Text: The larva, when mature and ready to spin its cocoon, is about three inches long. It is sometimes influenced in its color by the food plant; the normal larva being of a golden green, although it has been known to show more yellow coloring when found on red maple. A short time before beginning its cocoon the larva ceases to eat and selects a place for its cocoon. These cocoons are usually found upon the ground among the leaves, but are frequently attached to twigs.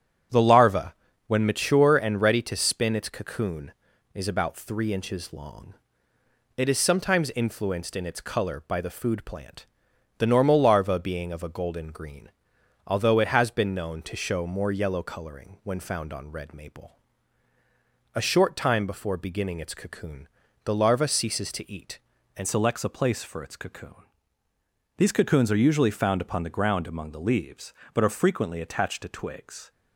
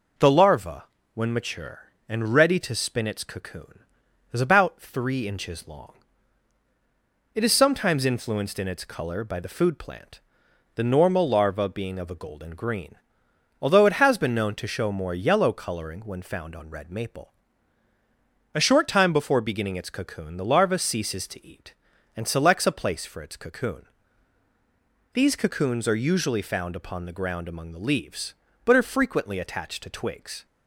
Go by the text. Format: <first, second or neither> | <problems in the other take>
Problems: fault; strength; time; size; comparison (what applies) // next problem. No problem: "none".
second | starts louder than the rest; strong; until 1.6 s; 8.5 dB // pauses between "cocoon" and "the"; slight; at 20.2 s; 0.36 s long // changes voice at "selects"; from 22.4 s on; 7.3 s long